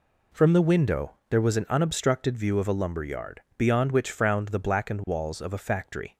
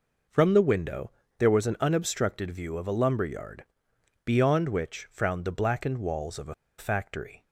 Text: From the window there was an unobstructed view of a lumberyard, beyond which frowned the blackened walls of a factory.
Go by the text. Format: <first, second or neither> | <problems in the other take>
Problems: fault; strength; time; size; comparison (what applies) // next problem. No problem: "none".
first | pauses between "window" and "there"; slight; at 1.1 s; 0.28 s long; slight in the first // pauses between "a" and "factory"; slight; at 6.5 s; 0.24 s long